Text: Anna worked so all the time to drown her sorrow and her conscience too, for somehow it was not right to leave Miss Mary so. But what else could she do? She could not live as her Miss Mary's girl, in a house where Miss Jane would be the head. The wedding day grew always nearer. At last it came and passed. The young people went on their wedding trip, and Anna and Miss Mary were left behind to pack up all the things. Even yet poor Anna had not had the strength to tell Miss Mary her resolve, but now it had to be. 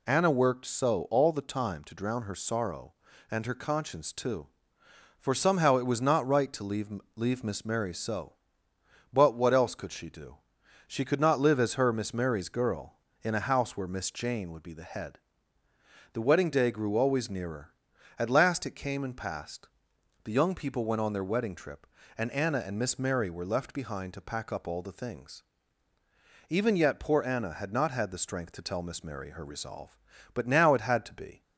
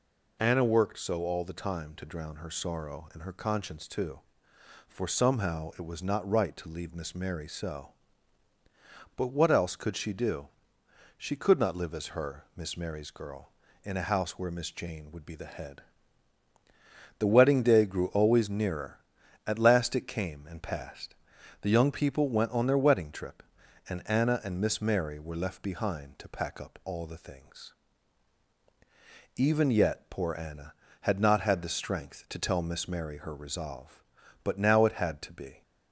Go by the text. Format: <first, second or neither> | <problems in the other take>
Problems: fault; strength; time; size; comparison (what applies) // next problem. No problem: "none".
second | says "leave" twice; at 7.1 s